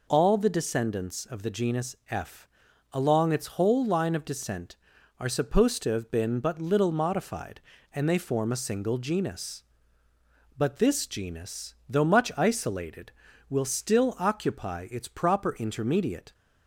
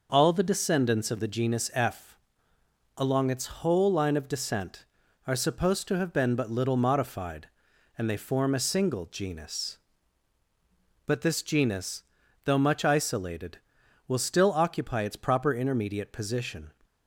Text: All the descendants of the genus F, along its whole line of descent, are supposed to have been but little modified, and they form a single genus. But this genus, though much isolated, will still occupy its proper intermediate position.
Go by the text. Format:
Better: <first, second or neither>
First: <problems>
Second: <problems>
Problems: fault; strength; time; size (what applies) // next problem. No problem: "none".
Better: second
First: stops before "position"; at 16.3 s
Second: none